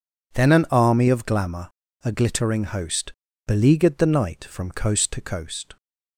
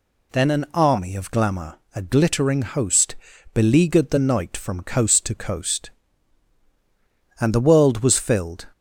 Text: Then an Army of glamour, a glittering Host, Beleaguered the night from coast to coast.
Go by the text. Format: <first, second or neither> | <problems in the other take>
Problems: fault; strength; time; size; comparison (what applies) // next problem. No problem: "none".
first | goes on to say "And the world was filled"; noticeable; from 7.4 s on; 1.2 s long